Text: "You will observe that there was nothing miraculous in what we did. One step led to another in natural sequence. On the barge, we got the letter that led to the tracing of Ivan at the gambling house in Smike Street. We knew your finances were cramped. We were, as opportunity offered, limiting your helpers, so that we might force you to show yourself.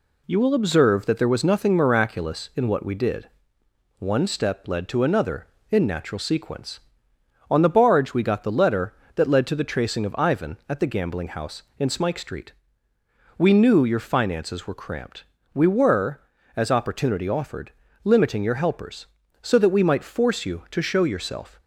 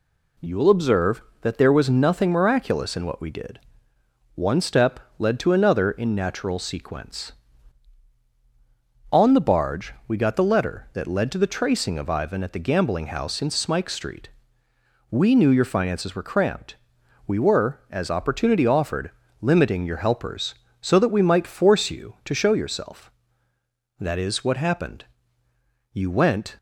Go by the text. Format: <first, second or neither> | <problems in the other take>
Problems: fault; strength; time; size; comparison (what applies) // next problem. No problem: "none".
first | pauses between "step" and "led"; slight; at 4.9 s; 0.18 s long // goes on to say "That is what happened You went"; strong; from 23.9 s on; 2.5 s long